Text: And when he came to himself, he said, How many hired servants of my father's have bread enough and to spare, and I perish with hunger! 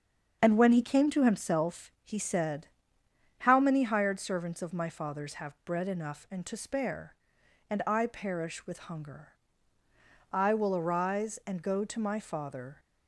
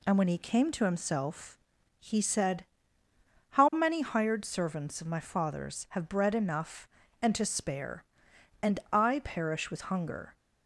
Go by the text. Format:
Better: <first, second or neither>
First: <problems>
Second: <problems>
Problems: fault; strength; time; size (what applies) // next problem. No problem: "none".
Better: second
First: starts louder than the rest; until 1.4 s; 7 dB // goes on to say "I will arise and go to my father"; strong; from 10.3 s on; 2.4 s long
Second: none